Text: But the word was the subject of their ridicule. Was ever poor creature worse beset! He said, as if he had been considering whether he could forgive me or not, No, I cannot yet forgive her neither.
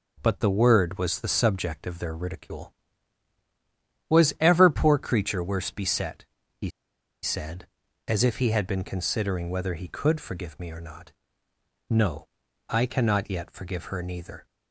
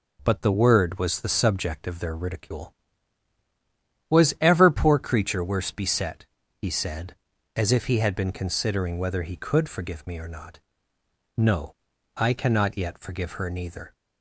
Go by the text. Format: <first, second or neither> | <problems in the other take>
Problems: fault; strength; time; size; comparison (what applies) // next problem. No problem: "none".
second | pauses between "He" and "said"; noticeable; at 6.6 s; 0.54 s long